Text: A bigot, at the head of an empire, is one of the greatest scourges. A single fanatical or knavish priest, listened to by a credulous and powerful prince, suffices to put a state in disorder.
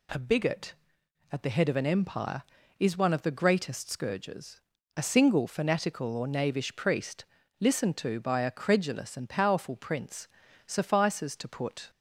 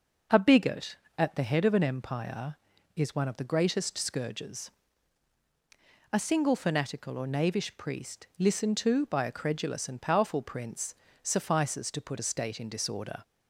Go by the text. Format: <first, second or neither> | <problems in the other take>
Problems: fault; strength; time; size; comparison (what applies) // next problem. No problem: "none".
second | stops before "a state in disorder"; at 11.9 s